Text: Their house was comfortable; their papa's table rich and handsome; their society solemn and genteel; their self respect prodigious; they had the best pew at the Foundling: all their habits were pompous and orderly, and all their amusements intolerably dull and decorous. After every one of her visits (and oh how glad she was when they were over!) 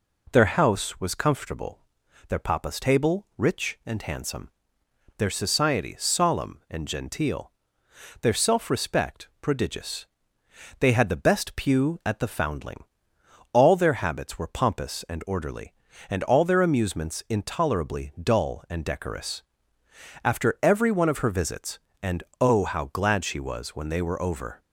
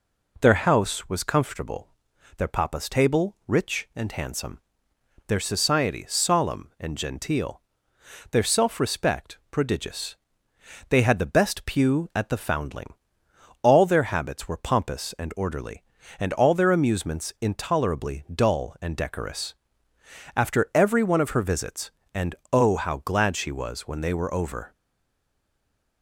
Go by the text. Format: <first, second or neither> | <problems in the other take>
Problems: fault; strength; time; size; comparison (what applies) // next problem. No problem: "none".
first | pauses between "and" and "oh"; slight; at 22.3 s; 0.20 s long; slight in the first // stays silent after the last word; noticeable; from 24.7 s on; 1.3 s long